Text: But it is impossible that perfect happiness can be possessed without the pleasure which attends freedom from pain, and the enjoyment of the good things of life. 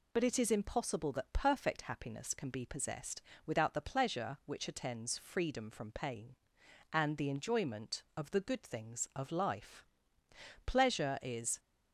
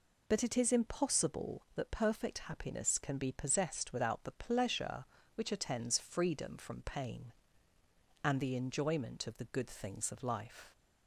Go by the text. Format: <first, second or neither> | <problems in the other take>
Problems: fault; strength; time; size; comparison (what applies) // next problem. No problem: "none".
second | pauses between "possessed" and "without"; slight; at 3.2 s; 0.24 s long // goes on to say "Pleasure is"; noticeable; from 10.6 s on; 0.94 s long